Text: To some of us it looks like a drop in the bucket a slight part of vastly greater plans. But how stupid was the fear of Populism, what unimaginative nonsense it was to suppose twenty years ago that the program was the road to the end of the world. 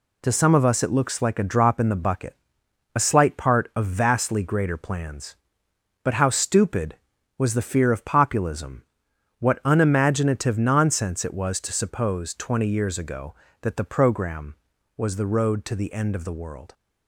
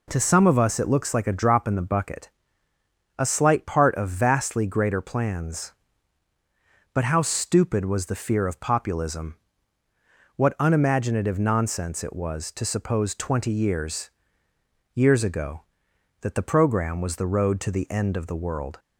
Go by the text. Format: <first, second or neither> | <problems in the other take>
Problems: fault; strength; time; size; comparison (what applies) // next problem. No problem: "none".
first | pauses between "bucket" and "a"; noticeable; at 2.3 s; 0.88 s long; noticeable in the first // says "years" twice; at 14.9 s